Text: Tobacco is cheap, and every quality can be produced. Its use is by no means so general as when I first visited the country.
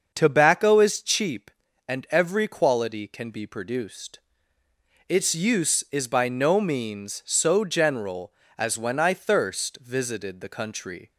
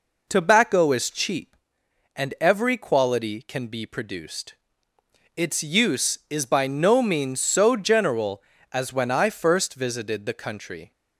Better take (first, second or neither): second